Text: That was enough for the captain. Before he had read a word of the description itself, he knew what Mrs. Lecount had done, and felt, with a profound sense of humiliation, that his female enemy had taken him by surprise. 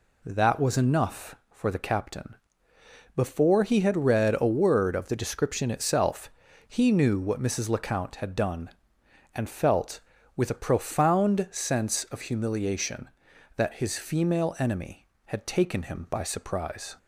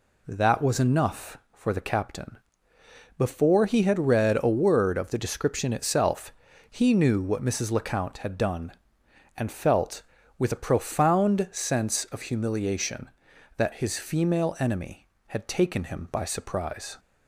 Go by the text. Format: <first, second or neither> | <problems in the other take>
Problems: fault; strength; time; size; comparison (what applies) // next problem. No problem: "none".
neither | none